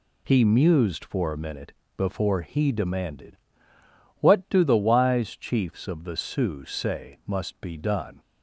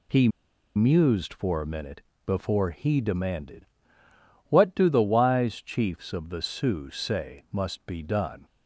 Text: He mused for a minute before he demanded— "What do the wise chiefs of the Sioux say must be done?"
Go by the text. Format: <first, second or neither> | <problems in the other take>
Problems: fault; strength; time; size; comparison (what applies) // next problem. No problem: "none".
first | pauses between "He" and "mused"; noticeable; at 0.2 s; 0.47 s long // pauses between "minute" and "before"; slight; at 2.0 s; 0.24 s long; slight in the first